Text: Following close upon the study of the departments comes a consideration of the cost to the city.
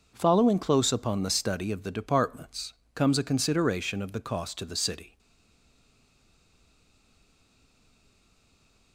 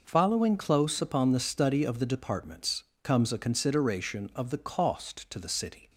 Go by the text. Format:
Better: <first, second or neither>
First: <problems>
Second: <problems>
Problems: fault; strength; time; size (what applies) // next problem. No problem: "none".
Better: second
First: pauses between "departments" and "comes"; slight; at 2.7 s; 0.22 s long // stays silent after the last word; strong; from 5.1 s on; 3.8 s long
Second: pauses between "departments" and "comes"; slight; at 2.8 s; 0.18 s long